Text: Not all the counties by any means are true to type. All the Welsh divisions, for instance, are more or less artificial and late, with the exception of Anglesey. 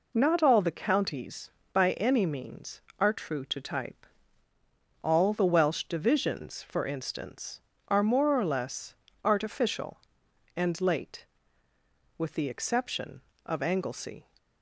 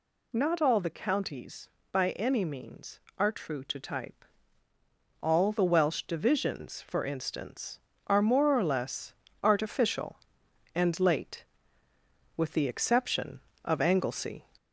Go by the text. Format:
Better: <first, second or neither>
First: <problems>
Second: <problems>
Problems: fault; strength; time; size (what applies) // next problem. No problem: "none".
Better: first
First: pauses between "less" and "artificial"; slight; at 8.9 s; 0.30 s long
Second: gets louder; slight; throughout; 2 dB // pauses between "less" and "artificial"; slight; at 9.1 s; 0.30 s long